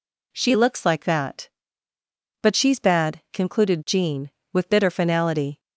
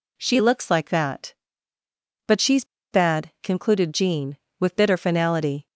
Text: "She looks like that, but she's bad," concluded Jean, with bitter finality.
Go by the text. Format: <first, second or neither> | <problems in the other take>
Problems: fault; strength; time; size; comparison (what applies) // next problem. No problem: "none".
first | pauses between "she's" and "bad"; slight; at 2.6 s; 0.28 s long